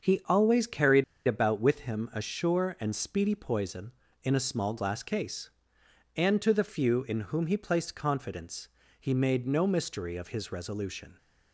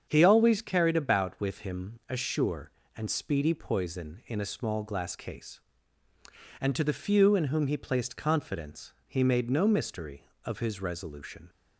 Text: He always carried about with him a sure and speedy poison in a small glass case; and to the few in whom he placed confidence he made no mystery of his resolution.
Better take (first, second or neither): second